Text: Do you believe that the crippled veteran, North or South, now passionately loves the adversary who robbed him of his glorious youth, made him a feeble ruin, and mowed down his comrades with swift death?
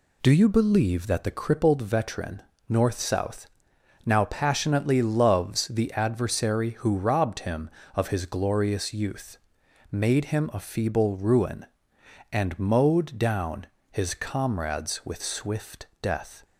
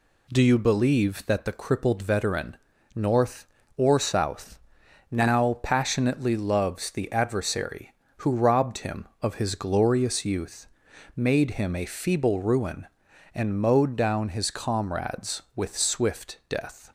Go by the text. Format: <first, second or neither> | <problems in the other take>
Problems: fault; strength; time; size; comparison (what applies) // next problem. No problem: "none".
second | skips "or"; at 2.9 s // pauses between "down" and "his"; slight; at 13.6 s; 0.26 s long // pauses between "swift" and "death"; slight; at 15.8 s; 0.16 s long